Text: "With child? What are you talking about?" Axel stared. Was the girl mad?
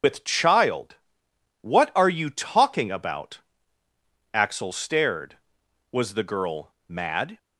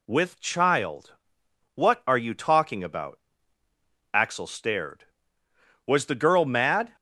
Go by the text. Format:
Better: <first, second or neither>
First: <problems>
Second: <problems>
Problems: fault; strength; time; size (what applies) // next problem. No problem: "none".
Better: second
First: loses the start of "With"; at 0.0 s; 140 ms // starts louder than the rest; until 1.7 s; 6.5 dB // pauses between "girl" and "mad"; slight; at 6.7 s; 0.16 s long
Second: none